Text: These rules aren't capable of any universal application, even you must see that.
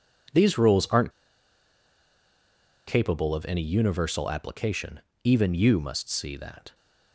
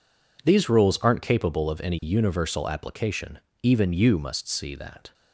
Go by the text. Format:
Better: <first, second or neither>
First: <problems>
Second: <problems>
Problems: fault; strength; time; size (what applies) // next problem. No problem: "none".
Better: second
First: pauses between "aren't" and "capable"; strong; at 1.1 s; 1.7 s long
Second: none